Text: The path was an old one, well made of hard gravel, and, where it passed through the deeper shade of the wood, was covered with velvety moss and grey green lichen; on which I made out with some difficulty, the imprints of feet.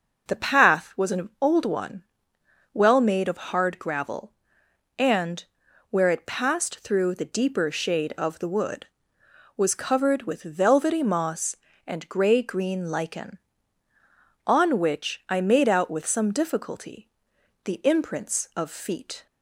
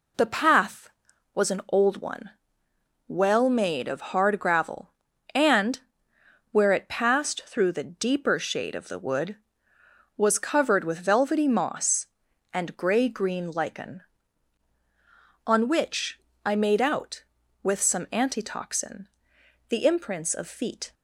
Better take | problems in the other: first | pauses between "which" and "I"; slight; at 16.1 s; 0.28 s long // says "antitoxin" for "difficulty"; at 18.1 s

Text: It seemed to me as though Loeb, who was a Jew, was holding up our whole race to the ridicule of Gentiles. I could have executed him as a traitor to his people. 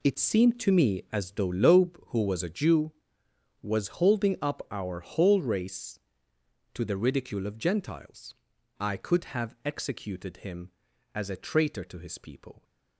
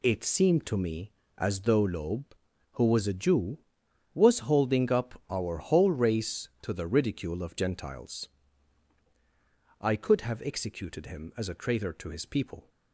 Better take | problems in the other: second | gets quieter; strong; throughout; 13 dB

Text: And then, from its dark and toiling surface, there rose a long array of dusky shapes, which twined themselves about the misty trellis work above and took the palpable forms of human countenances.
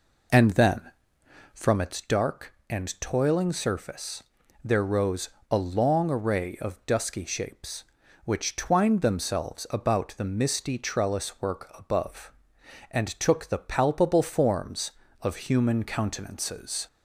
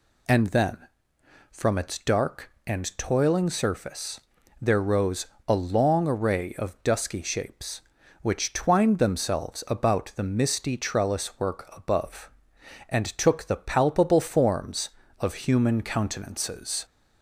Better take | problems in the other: second | starts louder than the rest; noticeable; until 1.9 s; 4 dB // pauses between "rose" and "a"; slight; at 5.2 s; 0.22 s long; slight in the second

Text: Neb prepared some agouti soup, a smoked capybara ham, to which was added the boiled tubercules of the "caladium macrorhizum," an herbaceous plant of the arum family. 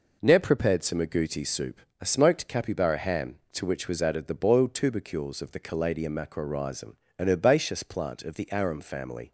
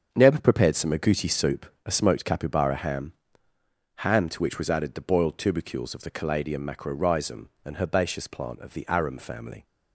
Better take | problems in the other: first | starts louder than the rest; strong; until 1.1 s; 7 dB // says "ham" twice; at 3.9 s

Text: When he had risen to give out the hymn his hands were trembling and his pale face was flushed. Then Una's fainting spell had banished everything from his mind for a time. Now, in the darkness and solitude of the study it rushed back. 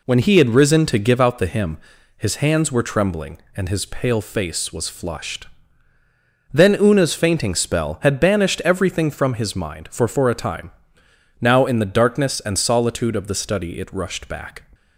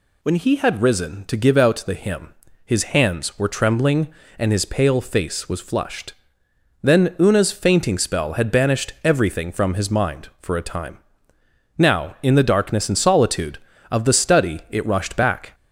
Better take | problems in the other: second | pauses between "hymn" and "his"; at 1.7 s; 0.40 s long; slight in the second // says "for" twice; at 10.0 s

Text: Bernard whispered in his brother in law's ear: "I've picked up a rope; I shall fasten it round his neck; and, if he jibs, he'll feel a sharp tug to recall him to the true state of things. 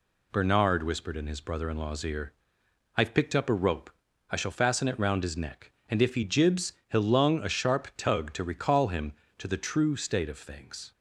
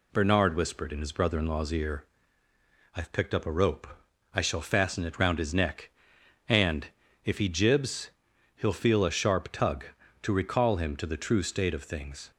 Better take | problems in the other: second | says "lung" for "feel"; at 7.0 s

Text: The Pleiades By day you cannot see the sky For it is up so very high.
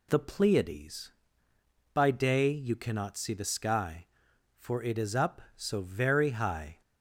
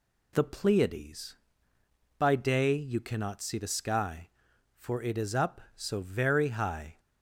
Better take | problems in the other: neither | none

